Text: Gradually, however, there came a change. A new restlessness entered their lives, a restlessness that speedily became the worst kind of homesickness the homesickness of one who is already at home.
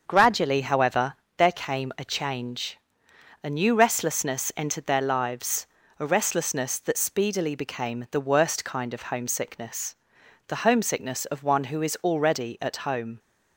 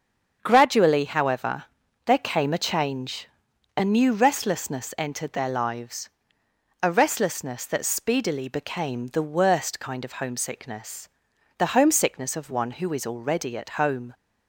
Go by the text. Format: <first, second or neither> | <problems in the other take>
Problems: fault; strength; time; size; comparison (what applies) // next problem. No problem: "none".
neither | starts louder than the rest; the same in both // pauses between "homesickness" and "the"; noticeable; the same in both